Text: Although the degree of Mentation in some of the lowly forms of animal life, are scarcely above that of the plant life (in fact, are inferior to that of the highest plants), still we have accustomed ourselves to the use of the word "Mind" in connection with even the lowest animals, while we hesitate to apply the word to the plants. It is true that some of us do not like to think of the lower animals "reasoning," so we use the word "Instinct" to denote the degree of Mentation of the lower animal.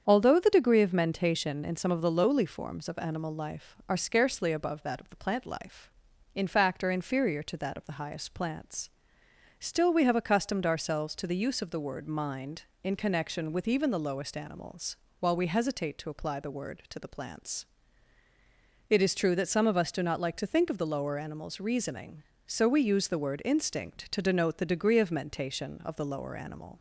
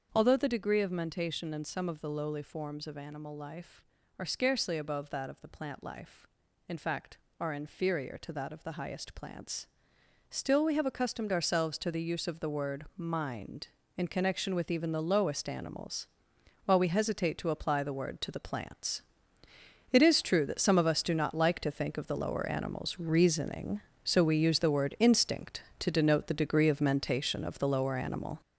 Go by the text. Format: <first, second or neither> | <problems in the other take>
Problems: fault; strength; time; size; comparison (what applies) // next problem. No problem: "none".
first | gets louder; strong; throughout; 7 dB // starts louder than the rest; until 1.1 s; 6.5 dB; strong in the first